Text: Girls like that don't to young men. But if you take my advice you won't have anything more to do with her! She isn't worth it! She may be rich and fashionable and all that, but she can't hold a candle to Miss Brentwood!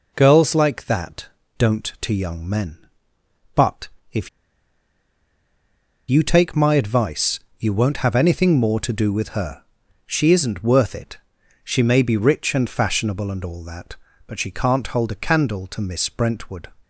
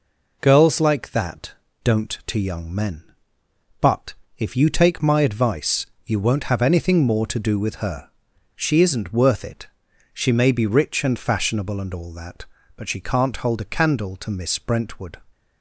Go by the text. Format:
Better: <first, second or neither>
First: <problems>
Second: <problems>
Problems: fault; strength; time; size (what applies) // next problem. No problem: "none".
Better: second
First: pauses between "that" and "don't"; slight; at 1.2 s; 0.28 s long // pauses between "But" and "if"; slight; at 3.8 s; 0.22 s long // pauses between "if" and "you"; strong; at 4.2 s; 1.7 s long // pauses between "advice" and "you"; slight; at 7.3 s; 0.20 s long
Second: pauses between "that" and "don't"; slight; at 1.5 s; 0.28 s long // pauses between "But" and "if"; slight; at 4.1 s; 0.22 s long // pauses between "advice" and "you"; slight; at 5.8 s; 0.20 s long